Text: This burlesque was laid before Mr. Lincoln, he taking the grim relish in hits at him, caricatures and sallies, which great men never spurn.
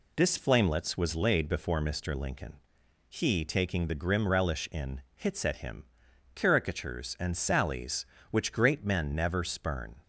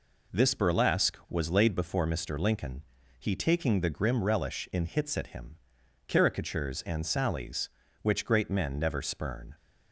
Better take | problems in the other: second | says "flamelets" for "burlesque"; at 0.3 s

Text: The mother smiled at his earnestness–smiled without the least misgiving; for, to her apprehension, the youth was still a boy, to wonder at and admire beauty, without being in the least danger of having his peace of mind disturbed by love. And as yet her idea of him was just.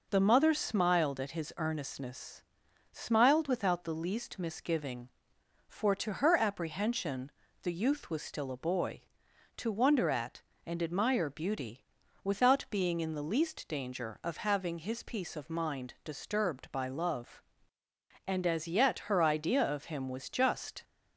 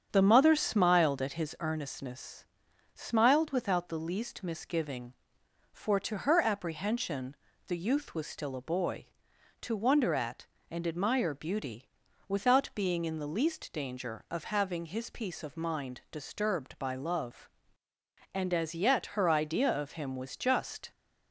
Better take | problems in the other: first | starts louder than the rest; strong; until 1.5 s; 8 dB

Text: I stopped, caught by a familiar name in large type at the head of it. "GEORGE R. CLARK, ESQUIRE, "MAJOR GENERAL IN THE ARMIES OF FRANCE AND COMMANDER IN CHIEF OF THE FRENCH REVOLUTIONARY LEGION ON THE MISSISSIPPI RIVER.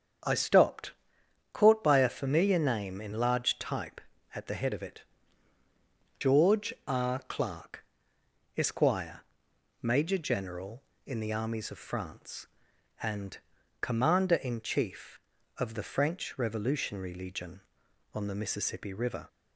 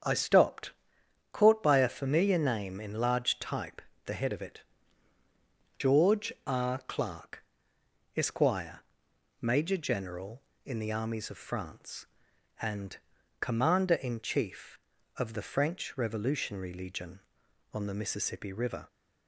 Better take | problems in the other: first | starts louder than the rest; strong; until 1.6 s; 7.5 dB; strong in the first // skips "at"; at 3.9 s // pauses between "AND" and "COMMANDER"; at 12.9 s; 0.42 s long; also in the first

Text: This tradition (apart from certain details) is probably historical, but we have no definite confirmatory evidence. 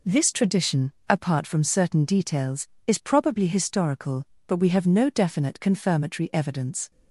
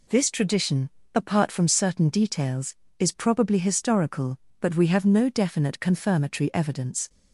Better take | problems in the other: neither | none

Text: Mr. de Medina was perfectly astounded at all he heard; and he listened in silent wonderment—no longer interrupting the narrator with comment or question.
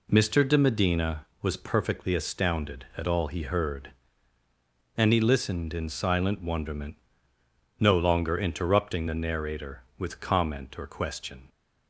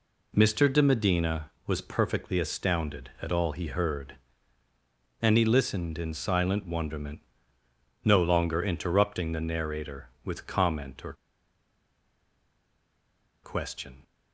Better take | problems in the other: first | pauses between "or" and "question"; strong; at 11.1 s; 2.2 s long

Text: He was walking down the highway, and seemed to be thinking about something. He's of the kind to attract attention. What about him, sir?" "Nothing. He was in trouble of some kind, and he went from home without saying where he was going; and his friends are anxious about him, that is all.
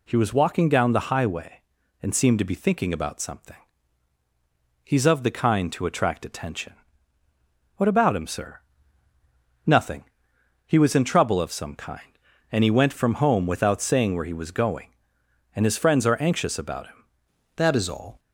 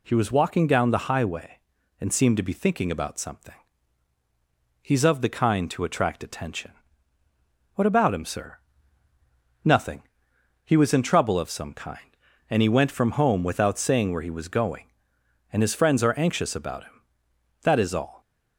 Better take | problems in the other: second | changes voice at "that"; from 17.5 s on; 0.6 s long

